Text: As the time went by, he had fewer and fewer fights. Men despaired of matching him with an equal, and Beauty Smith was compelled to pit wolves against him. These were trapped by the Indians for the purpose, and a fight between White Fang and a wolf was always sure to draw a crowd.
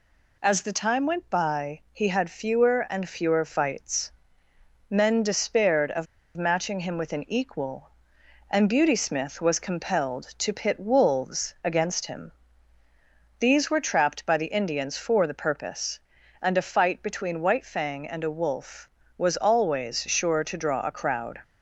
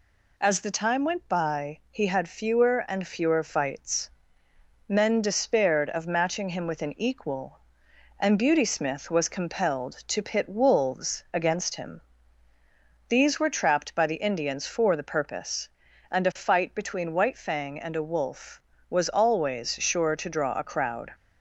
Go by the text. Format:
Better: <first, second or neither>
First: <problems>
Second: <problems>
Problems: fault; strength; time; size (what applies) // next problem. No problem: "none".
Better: second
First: pauses between "of" and "matching"; slight; at 6.0 s; 0.31 s long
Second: none